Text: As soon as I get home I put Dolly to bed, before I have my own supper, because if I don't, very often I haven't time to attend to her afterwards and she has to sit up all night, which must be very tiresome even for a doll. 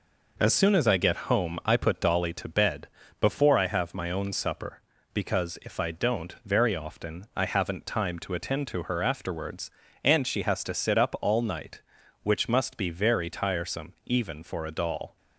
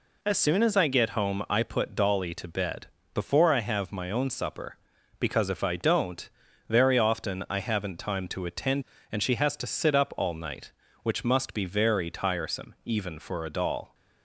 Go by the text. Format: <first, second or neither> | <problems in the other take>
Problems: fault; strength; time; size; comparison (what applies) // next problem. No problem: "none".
first | skips "to her afterwards"; at 8.9 s